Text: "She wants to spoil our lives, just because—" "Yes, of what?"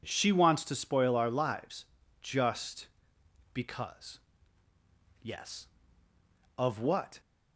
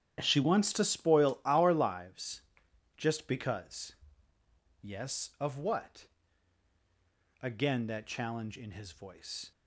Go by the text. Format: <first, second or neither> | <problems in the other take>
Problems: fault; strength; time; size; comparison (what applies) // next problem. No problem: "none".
first | starts louder than the rest; strong; until 1.2 s; 9.5 dB // goes on to say "Again that challenge in his voice"; strong; from 7.4 s on; 2.1 s long